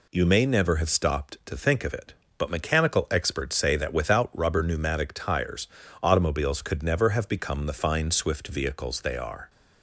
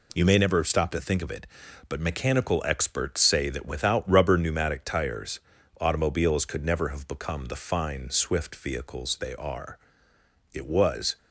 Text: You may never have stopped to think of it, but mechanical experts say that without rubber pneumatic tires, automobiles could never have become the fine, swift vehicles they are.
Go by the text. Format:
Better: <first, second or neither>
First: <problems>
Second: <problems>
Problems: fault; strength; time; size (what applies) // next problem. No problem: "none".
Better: first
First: none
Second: goes on to say "It was"; noticeable; from 10.5 s on; 0.64 s long